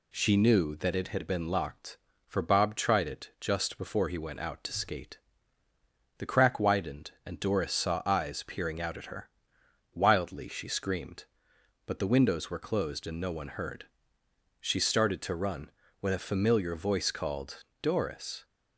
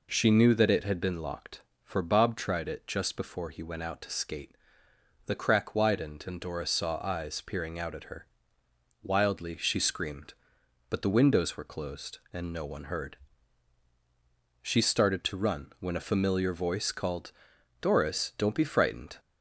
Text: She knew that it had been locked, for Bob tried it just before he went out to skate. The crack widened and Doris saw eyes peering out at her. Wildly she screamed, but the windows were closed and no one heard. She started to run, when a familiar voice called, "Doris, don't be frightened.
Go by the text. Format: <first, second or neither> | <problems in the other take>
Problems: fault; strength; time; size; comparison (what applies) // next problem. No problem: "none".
second | stops before "don't be frightened"; at 18.4 s